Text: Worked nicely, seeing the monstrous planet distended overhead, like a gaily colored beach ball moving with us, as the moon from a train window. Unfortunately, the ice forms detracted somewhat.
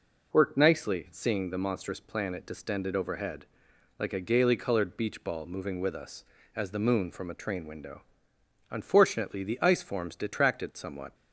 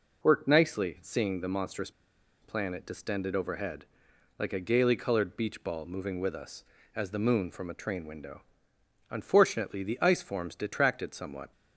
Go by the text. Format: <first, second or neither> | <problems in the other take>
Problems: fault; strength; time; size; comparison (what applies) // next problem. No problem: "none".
first | pauses between "monstrous" and "planet"; noticeable; at 1.9 s; 0.51 s long